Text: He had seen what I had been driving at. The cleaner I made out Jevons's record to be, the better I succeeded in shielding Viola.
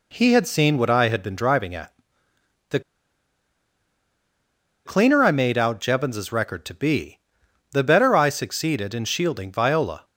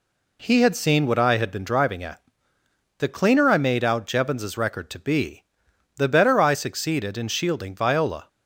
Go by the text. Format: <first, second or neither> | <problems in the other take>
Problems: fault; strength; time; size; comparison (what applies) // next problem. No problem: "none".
second | pauses between "The" and "cleaner"; strong; at 2.7 s; 2.0 s long